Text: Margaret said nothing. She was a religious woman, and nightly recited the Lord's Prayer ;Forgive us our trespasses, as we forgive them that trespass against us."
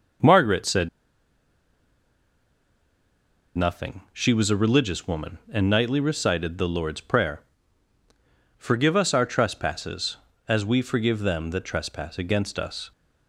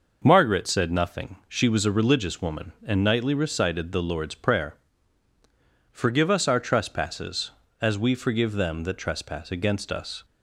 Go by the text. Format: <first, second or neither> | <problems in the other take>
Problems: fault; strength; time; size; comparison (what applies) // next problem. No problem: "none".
second | pauses between "said" and "nothing"; strong; at 0.8 s; 2.6 s long